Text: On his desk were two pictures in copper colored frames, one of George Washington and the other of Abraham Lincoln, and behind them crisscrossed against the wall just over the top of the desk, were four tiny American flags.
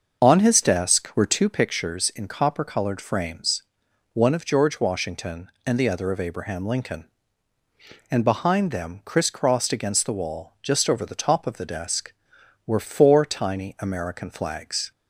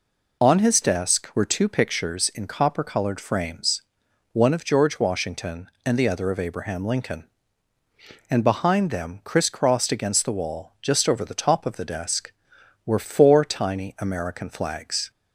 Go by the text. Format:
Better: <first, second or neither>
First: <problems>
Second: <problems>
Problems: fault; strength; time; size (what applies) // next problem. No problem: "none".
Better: second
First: starts louder than the rest; until 1.5 s; 6.5 dB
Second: none